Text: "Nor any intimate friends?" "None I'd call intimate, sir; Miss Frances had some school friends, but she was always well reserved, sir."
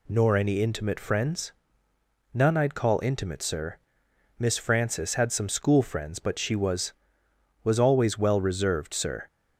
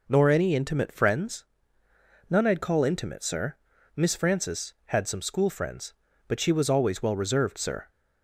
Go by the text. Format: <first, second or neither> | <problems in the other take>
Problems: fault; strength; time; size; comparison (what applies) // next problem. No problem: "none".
second | says "was" twice; at 7.6 s